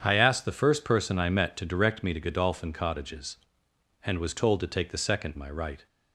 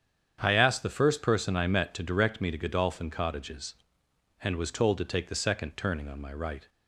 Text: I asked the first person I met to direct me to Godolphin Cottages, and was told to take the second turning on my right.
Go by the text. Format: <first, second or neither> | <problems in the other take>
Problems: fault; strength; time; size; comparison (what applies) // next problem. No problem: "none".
second | starts louder than the rest; strong; until 1.0 s; 8 dB; strong in the second // skips "turning on"; at 5.3 s